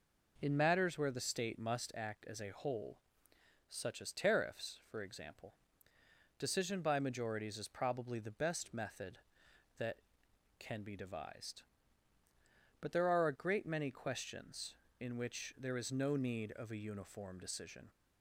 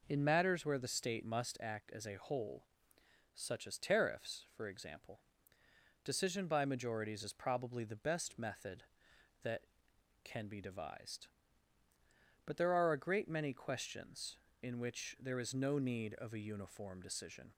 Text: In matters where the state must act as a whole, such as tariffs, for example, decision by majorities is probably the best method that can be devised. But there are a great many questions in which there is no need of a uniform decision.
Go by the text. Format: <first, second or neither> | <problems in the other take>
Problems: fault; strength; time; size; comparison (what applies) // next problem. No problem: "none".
neither | none